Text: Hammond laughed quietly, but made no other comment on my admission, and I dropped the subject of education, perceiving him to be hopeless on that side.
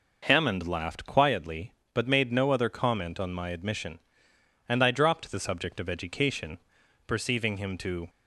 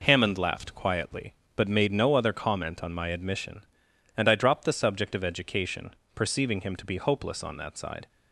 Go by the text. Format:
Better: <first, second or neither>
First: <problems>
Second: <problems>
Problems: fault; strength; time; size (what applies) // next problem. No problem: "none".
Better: second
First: stops before "be hopeless on that side"; at 8.0 s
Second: none